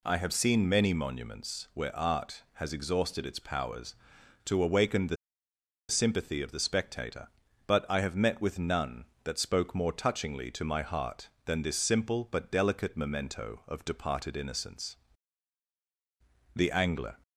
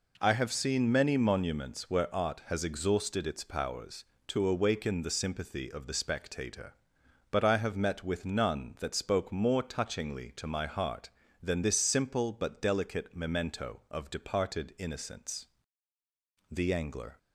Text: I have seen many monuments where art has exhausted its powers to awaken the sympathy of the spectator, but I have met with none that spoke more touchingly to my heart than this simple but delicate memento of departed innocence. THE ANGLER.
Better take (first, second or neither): second